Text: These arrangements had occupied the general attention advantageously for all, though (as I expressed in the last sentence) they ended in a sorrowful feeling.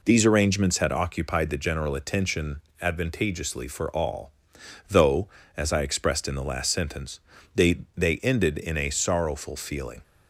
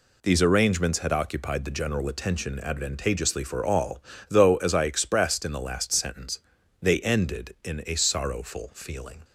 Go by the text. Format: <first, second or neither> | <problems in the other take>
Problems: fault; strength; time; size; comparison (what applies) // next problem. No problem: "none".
second | pauses between "attention" and "advantageously"; slight; at 2.5 s; 0.20 s long // says "they" twice; at 7.9 s